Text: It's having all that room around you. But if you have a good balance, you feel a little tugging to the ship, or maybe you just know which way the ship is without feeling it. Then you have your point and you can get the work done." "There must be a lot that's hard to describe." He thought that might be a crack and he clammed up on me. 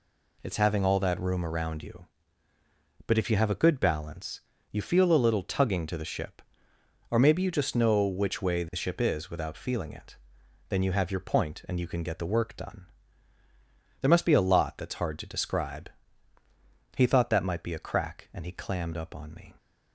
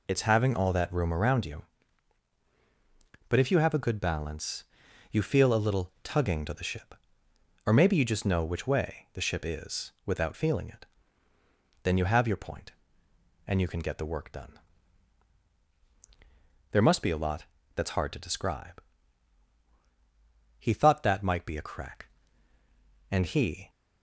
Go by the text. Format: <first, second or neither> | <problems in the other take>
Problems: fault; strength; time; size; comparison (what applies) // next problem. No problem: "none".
first | pauses between "lot" and "that's"; slight; at 17.4 s; 0.30 s long // stops before "clammed up on me"; at 23.6 s